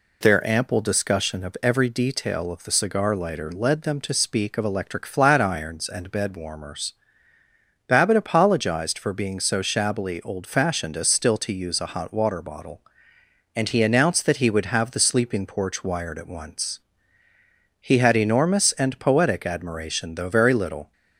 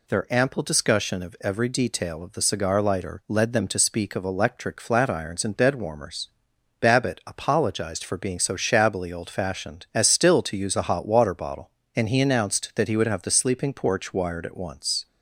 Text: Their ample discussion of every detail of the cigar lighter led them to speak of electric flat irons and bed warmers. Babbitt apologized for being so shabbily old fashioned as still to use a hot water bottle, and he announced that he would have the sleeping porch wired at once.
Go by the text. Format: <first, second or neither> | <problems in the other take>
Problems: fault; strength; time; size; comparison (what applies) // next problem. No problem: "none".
second | goes on to say "He had enormous and poetic admiration though very little"; strong; from 17.7 s on; 3.1 s long